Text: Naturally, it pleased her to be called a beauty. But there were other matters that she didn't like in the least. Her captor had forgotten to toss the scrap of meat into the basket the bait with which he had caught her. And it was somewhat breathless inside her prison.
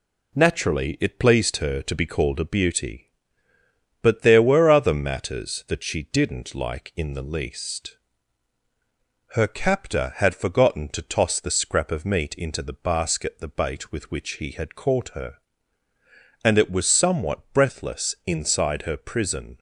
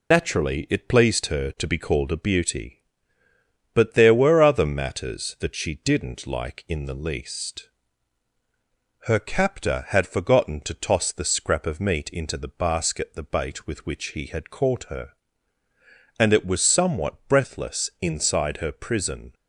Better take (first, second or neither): first